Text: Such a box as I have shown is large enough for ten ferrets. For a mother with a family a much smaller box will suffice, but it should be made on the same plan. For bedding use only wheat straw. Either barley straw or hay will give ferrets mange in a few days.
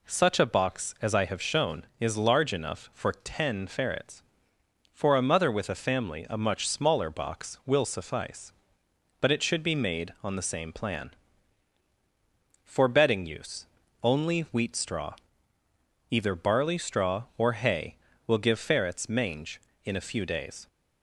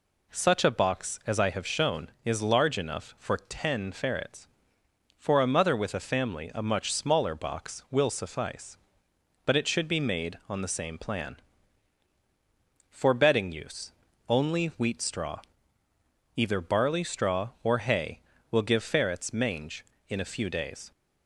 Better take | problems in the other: neither | pauses between "use" and "only"; the same in both

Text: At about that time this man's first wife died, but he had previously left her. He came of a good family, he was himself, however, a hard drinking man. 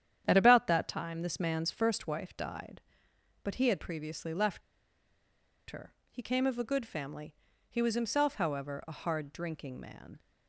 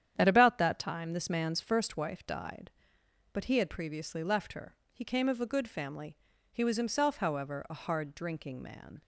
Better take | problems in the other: second | starts louder than the rest; strong; until 1.2 s; 9.5 dB; strong in the second // pauses between "left" and "her"; at 4.6 s; 1.1 s long

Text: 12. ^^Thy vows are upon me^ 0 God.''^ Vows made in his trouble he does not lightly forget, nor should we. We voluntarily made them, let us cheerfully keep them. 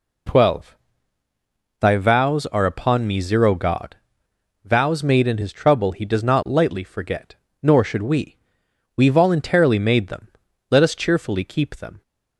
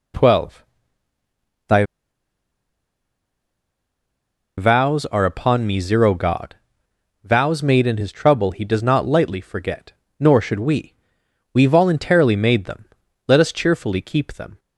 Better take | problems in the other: first | pauses between "Thy" and "vows"; strong; at 1.8 s; 2.7 s long

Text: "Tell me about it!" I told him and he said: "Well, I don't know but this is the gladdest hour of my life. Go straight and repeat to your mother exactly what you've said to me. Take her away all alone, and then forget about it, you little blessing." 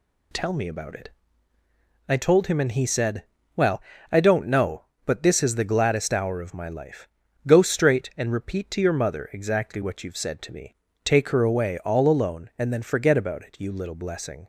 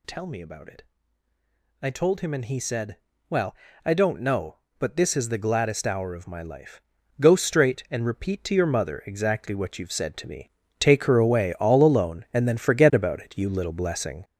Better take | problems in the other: first | gets louder; throughout; 6.5 dB

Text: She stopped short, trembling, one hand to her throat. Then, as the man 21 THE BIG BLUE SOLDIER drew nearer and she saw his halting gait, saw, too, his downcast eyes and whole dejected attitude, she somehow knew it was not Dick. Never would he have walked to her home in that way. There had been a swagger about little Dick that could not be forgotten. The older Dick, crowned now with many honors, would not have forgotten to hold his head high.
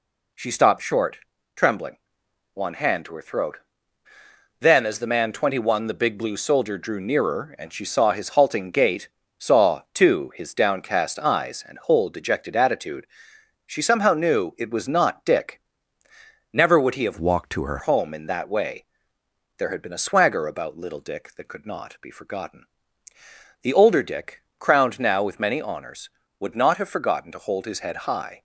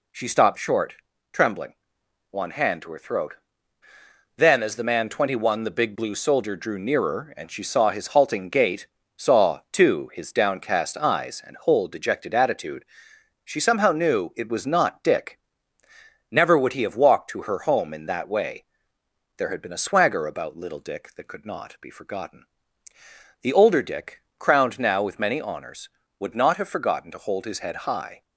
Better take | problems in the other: second | changes voice from "walked" to "her"; from 17.1 to 17.7 s; 0.6 s long

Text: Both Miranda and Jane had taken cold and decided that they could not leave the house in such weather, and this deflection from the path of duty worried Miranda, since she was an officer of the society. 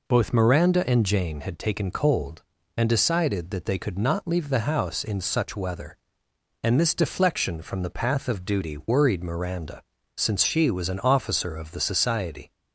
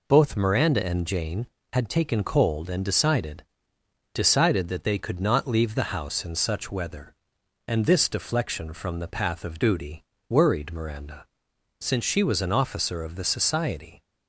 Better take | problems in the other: first | says "decided" twice; at 4.1 s // pauses between "duty" and "worried"; slight; at 10.0 s; 0.26 s long

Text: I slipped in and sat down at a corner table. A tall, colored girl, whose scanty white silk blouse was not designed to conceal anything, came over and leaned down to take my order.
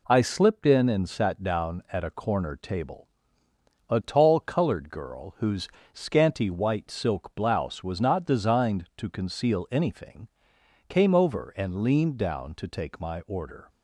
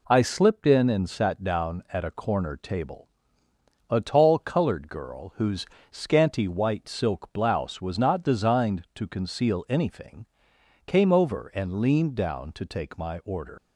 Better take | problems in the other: first | pauses between "whose" and "scanty"; slight; at 5.6 s; 0.26 s long; slight in the first // leaves "order" unfinished; at 13.5 s; 85 ms

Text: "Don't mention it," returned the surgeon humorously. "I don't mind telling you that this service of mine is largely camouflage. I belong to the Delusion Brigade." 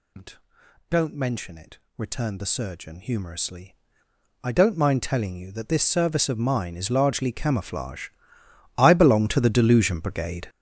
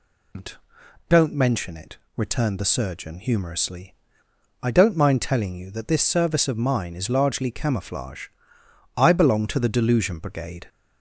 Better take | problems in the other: second | gets louder; strong; throughout; 11 dB

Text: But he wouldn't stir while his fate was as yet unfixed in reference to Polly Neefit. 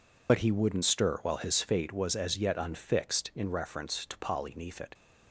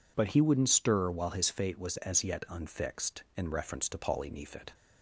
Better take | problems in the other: second | loses the start of "But"; at 0.2 s; 45 ms

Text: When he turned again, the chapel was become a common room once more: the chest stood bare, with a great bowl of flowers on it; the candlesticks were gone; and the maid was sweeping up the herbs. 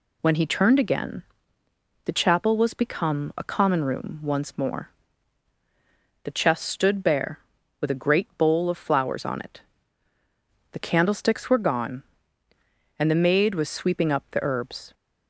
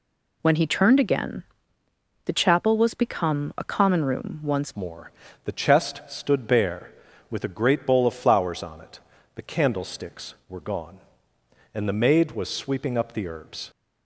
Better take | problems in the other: first | changes voice at "more"; from 4.7 s on; 9.0 s long

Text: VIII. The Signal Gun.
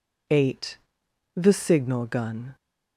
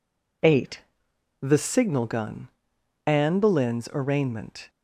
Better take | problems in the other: first | goes on to say "Anne Boleyn's arraignment"; from 3.0 s on; 1.6 s long

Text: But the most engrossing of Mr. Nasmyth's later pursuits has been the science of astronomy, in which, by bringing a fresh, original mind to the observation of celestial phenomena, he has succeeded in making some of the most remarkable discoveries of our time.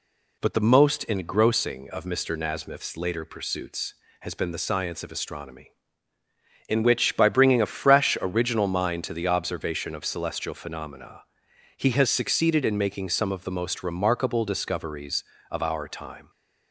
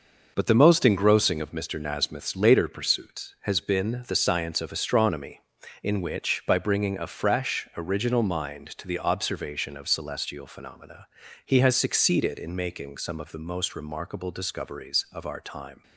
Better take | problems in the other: neither | none

